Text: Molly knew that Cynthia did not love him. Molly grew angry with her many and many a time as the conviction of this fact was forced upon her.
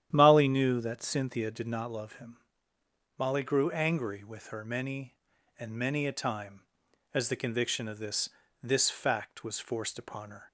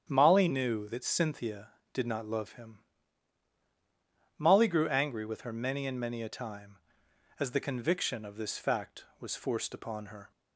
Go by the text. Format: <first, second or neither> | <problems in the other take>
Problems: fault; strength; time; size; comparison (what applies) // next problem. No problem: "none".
second | starts louder than the rest; strong; until 1.1 s; 10.5 dB; strong in the second // says "this" twice; at 8.6 s